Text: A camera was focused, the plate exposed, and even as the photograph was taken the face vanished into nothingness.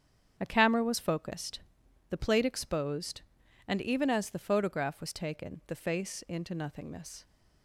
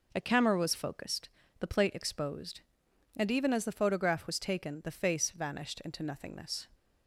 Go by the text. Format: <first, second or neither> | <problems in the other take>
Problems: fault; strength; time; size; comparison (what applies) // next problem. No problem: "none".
second | starts louder than the rest; strong; until 1.3 s; 8 dB // skips "vanished"; at 6.2 s